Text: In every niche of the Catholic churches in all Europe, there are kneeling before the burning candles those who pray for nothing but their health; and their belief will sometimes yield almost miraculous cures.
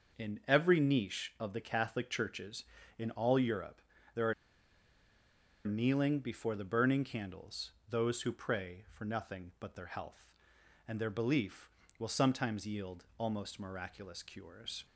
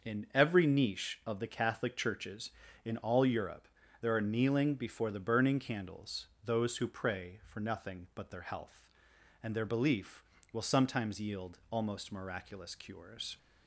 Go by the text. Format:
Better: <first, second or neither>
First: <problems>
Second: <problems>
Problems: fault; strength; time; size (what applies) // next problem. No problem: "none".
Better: second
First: starts louder than the rest; until 1.2 s; 6.5 dB // pauses between "are" and "kneeling"; strong; at 4.3 s; 1.3 s long // pauses between "candles" and "those"; slight; at 7.7 s; 0.16 s long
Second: starts louder than the rest; until 1.1 s; 6.5 dB // pauses between "candles" and "those"; slight; at 6.2 s; 0.16 s long